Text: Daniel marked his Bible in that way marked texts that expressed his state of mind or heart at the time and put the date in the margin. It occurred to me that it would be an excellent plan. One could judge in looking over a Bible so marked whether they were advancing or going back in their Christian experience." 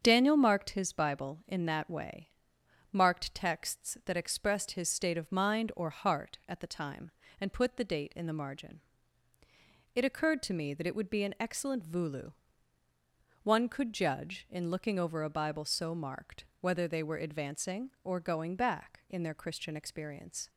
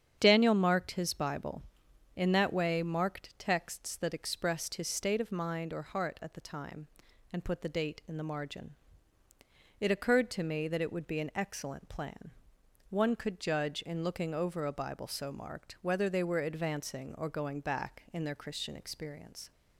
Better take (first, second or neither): second